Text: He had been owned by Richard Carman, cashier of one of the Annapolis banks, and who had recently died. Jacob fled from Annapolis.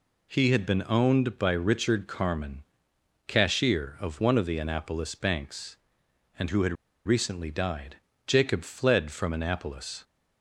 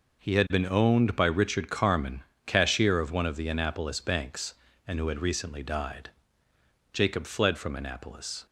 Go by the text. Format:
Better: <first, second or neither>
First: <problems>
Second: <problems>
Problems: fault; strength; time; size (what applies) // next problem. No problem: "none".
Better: second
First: pauses between "had" and "recently"; slight; at 6.7 s; 0.31 s long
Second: none